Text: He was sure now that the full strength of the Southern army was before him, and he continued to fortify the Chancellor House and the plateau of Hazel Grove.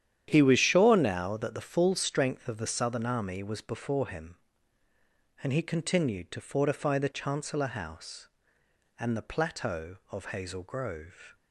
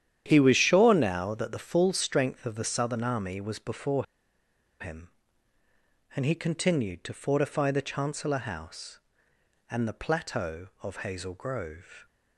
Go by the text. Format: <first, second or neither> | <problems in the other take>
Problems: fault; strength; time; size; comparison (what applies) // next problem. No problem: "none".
first | starts louder than the rest; strong; until 1.2 s; 10 dB; strong in the first // pauses between "before" and "him"; noticeable; at 4.0 s; 0.75 s long